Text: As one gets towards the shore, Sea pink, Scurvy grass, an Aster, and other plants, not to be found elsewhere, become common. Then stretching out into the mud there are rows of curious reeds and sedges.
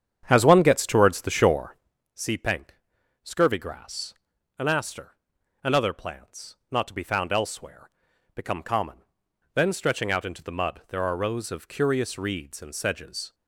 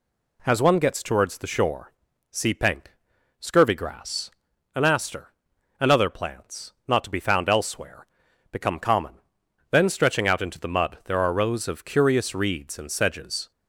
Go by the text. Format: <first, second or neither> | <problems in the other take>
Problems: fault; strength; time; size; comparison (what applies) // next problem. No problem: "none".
second | starts louder than the rest; strong; until 1.9 s; 8.5 dB